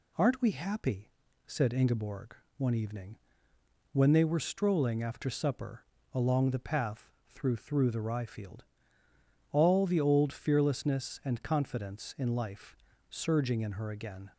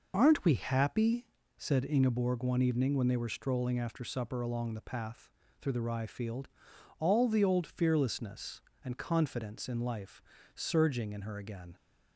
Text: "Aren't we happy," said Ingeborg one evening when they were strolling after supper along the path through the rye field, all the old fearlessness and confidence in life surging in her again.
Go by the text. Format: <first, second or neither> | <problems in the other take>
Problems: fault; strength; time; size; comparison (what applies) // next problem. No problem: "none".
second | pauses between "Ingeborg" and "one"; slight; at 2.3 s; 0.24 s long // pauses between "evening" and "when"; noticeable; at 3.1 s; 0.76 s long // pauses between "supper" and "along"; slight; at 5.8 s; 0.28 s long // pauses between "path" and "through"; slight; at 7.0 s; 0.22 s long; slight in the second // says "through" twice; at 7.5 s // pauses between "life" and "surging"; slight; at 12.7 s; 0.32 s long; slight in the second